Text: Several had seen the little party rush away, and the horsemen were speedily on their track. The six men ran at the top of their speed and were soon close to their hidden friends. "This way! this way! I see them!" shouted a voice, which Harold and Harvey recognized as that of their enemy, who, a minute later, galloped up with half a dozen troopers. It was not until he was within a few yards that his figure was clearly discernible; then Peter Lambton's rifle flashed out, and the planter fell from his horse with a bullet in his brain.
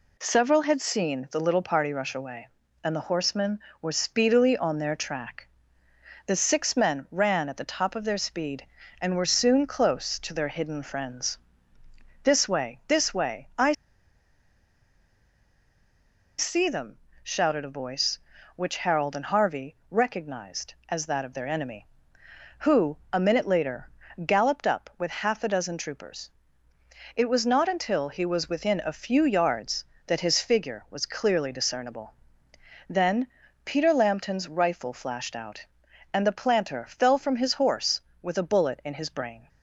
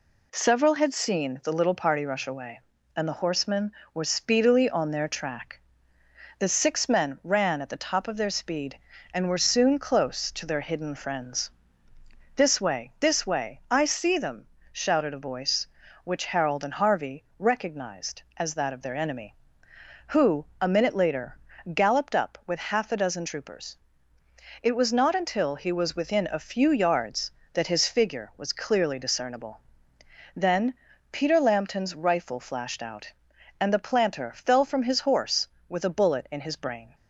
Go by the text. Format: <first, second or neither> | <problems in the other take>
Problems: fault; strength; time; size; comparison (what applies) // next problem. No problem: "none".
second | pauses between "I" and "see"; strong; at 13.7 s; 2.6 s long // pauses between "Harvey" and "recognized"; slight; at 19.7 s; 0.16 s long; slight in the second // pauses between "then" and "Peter"; at 33.2 s; 0.40 s long; also in the second